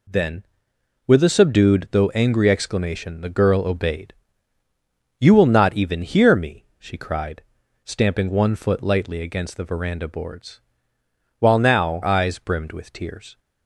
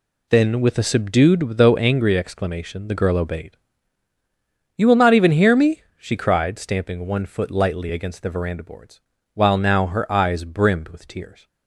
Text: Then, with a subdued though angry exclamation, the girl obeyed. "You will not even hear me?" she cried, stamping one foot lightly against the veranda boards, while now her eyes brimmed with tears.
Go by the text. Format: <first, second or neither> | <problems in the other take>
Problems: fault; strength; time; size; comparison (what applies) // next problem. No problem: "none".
second | skips "her"; at 12.0 s